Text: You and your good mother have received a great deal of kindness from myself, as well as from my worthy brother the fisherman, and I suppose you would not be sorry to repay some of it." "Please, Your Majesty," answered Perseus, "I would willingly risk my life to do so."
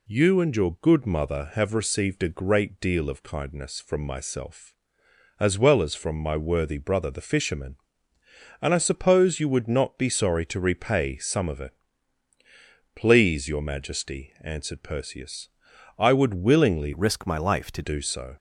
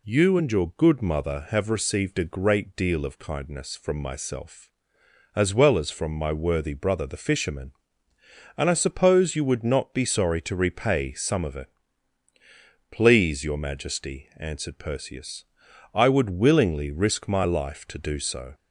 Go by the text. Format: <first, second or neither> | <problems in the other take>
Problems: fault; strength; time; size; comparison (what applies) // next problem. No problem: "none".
second | changes voice from "risk" to "to"; from 16.9 to 17.8 s; 0.9 s long